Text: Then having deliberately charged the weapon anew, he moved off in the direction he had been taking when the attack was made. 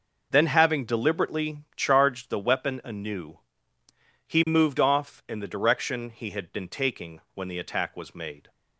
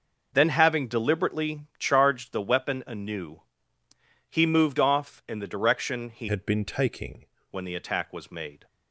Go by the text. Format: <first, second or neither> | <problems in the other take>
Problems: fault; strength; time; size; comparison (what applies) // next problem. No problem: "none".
first | changes voice from "had" to "taking"; from 6.2 to 7.2 s; 1.0 s long